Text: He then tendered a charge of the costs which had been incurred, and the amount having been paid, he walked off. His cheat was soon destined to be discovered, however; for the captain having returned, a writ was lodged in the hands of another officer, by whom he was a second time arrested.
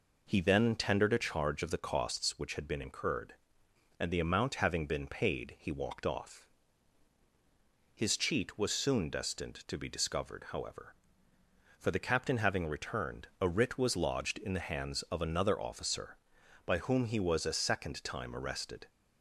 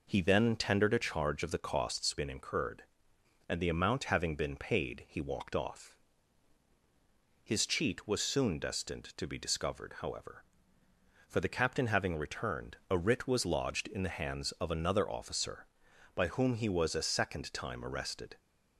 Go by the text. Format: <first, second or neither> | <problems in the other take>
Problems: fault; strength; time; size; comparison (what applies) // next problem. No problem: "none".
first | skips "which had"; at 2.1 s